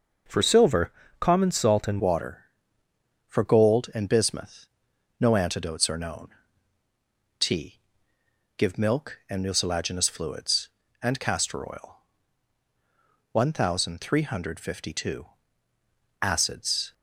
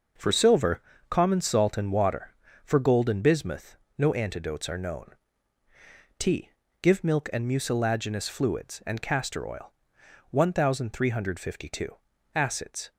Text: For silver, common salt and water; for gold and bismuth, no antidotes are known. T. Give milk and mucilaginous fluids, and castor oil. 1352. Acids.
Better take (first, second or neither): second